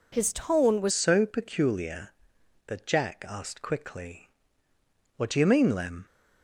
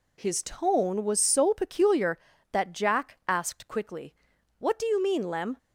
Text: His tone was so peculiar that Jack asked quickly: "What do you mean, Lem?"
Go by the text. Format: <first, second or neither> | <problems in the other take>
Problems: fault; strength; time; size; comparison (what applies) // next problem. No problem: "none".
second | changes voice at "so"; from 0.8 s on; 5.2 s long